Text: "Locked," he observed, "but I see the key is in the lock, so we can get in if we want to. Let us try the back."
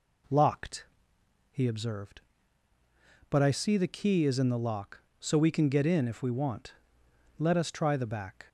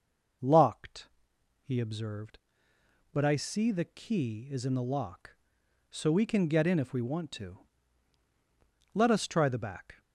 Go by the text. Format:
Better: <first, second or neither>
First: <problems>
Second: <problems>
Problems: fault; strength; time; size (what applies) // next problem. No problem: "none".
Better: second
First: skips "to"; at 7.0 s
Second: none